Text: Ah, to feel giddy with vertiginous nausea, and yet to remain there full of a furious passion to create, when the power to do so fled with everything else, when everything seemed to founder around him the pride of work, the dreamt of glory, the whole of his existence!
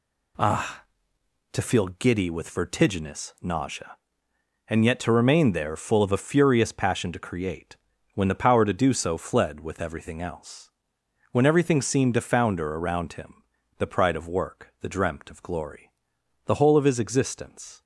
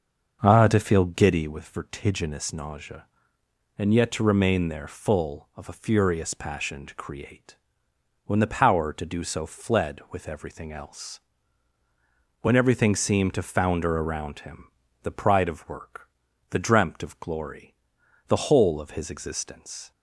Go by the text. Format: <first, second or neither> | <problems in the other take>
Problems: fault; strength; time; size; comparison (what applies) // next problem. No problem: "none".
first | starts louder than the rest; until 1.7 s; 6 dB // pauses between "him" and "the"; slight; at 14.6 s; 0.34 s long; slight in the first